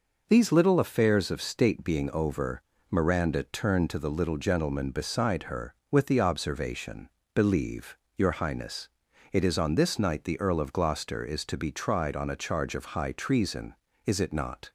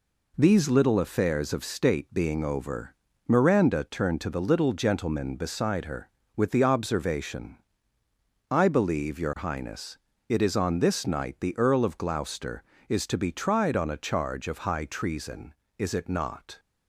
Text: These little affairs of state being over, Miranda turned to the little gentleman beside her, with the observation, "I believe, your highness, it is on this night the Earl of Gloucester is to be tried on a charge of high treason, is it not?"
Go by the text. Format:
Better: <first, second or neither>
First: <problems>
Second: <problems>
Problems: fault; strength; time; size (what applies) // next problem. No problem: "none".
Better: second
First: skips "I"; at 7.2 s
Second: none